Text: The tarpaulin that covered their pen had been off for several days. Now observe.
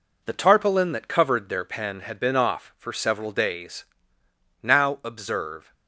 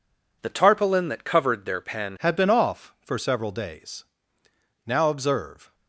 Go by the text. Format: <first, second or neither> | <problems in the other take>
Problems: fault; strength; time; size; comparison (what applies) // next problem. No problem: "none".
first | changes voice at "had"; from 2.1 s on; 3.6 s long